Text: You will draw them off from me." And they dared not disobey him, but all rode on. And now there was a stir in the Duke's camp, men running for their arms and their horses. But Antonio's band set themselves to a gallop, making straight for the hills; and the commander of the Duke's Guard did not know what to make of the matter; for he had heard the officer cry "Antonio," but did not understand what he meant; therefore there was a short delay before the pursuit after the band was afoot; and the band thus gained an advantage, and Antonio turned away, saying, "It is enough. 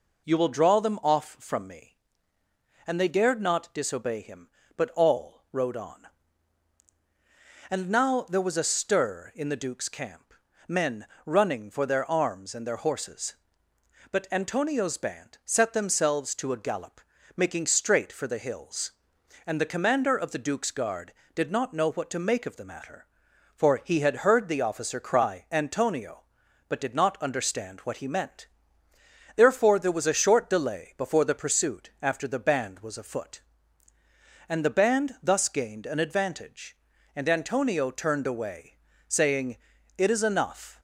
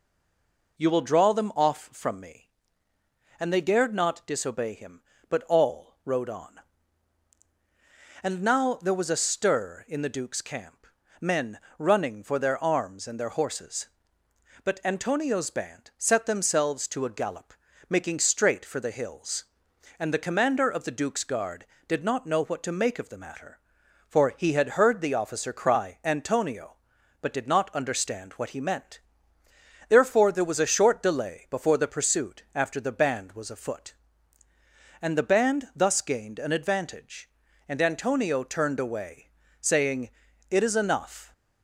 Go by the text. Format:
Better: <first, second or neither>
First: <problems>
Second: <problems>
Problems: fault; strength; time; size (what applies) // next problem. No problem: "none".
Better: first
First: pauses between "men" and "running"; slight; at 11.0 s; 0.20 s long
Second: stays silent before the first word; slight; until 0.7 s; 0.7 s long // pauses between "men" and "running"; slight; at 11.5 s; 0.20 s long